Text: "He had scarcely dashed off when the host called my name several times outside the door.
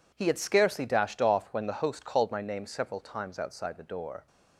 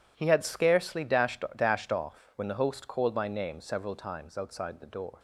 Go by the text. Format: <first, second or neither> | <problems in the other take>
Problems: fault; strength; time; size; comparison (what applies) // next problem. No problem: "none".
first | says "dashed" twice; at 1.5 s